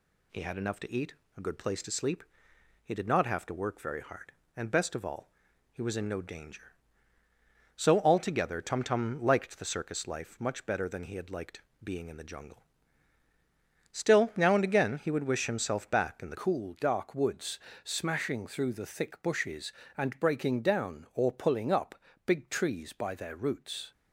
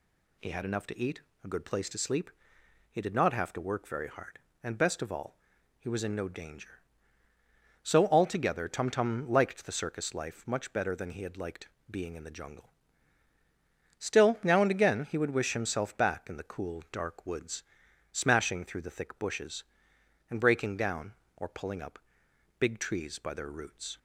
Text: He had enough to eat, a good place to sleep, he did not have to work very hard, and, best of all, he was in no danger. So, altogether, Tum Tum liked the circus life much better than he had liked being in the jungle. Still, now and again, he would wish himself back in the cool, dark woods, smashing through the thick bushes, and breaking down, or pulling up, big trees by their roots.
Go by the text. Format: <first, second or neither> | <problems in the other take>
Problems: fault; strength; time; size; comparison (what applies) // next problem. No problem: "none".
second | pauses between "liked" and "being"; slight; at 11.6 s; 0.22 s long; slight in the second // changes voice at "cool"; from 16.3 s on; 7.6 s long